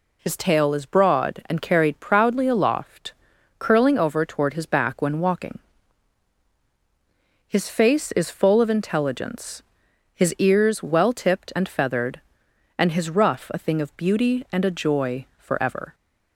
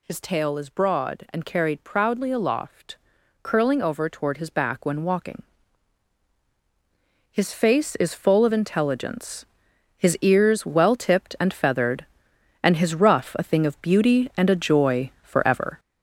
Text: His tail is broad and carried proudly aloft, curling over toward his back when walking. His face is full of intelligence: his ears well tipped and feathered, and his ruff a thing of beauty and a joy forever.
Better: first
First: none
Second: gets louder; throughout; 6.5 dB

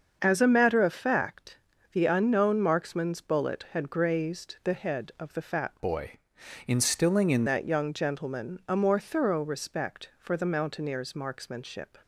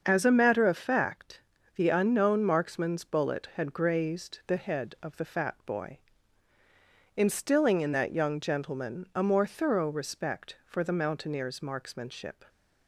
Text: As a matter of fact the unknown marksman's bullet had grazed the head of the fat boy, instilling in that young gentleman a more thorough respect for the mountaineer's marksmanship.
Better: second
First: starts louder than the rest; until 1.2 s; 6.5 dB // pauses between "fact" and "the"; at 1.5 s; 0.38 s long // changes voice from "boy" to "in"; from 5.7 to 7.4 s; 1.7 s long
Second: starts louder than the rest; until 1.0 s; 6.5 dB // pauses between "fact" and "the"; at 1.3 s; 0.38 s long

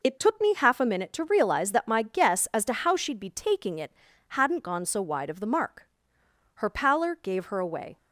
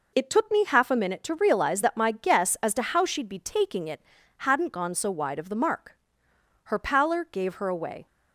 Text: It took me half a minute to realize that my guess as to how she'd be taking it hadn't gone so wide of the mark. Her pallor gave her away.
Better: neither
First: pauses between "it" and "hadn't"; slight; at 3.9 s; 0.36 s long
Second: pauses between "it" and "hadn't"; slight; at 4.0 s; 0.36 s long

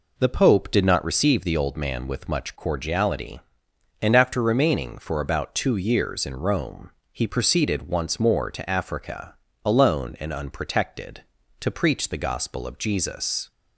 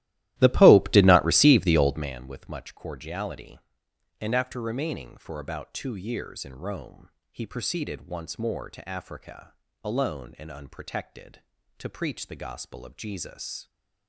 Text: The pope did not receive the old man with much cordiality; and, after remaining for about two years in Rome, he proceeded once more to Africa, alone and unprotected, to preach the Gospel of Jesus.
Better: first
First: none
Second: starts louder than the rest; strong; until 2.1 s; 15 dB

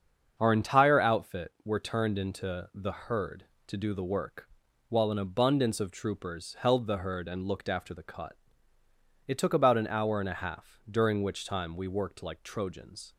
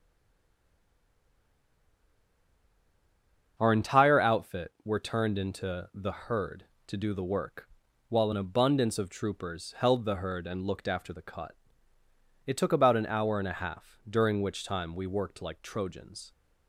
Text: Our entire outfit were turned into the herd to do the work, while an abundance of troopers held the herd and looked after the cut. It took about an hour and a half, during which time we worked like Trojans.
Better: first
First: starts louder than the rest; until 1.3 s; 7 dB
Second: stays silent before the first word; strong; until 3.5 s; 3.5 s long // starts louder than the rest; until 4.5 s; 7 dB

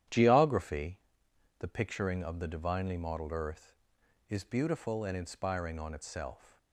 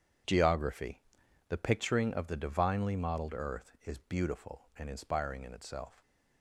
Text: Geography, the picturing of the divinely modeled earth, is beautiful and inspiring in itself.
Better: second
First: starts louder than the rest; strong; until 1.7 s; 11 dB // says "on" for "in"; at 5.7 s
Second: none

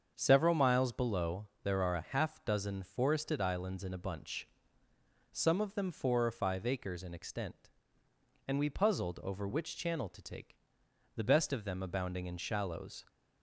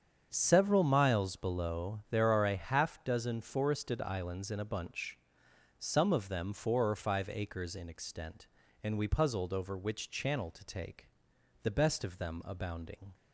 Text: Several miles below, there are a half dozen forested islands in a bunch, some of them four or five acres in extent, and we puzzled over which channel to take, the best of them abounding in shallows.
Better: first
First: starts louder than the rest; until 1.1 s; 7 dB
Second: starts louder than the rest; strong; until 1.3 s; 7.5 dB // stops before "in shallows"; at 13.1 s

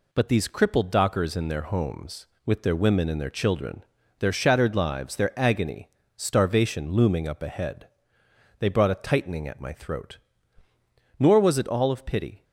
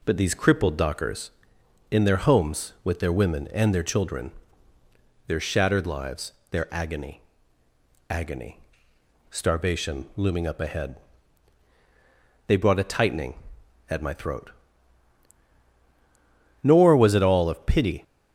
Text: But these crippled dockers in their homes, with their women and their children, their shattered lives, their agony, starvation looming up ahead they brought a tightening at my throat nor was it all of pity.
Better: first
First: pauses between "ahead" and "they"; noticeable; at 7.8 s; 0.72 s long // pauses between "throat" and "nor"; at 10.1 s; 1.0 s long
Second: says "agony" twice; at 8.0 s // pauses between "ahead" and "they"; strong; at 10.9 s; 1.5 s long // pauses between "throat" and "nor"; strong; at 14.5 s; 2.1 s long

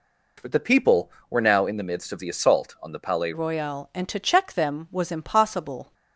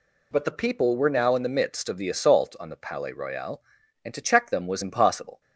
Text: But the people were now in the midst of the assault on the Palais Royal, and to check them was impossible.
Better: second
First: changes voice at "Royal"; from 3.3 s on; 2.6 s long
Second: none

